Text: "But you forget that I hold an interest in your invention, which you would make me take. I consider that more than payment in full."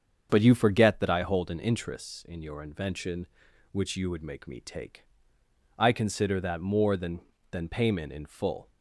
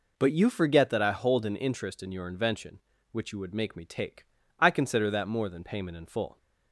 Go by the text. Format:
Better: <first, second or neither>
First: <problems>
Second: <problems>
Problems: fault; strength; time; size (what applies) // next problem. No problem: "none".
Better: second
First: starts louder than the rest; strong; until 1.3 s; 7.5 dB // says "than" twice; at 7.5 s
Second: none